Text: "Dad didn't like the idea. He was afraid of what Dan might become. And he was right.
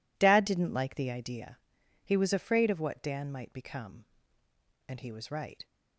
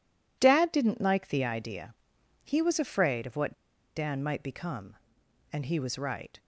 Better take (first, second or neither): first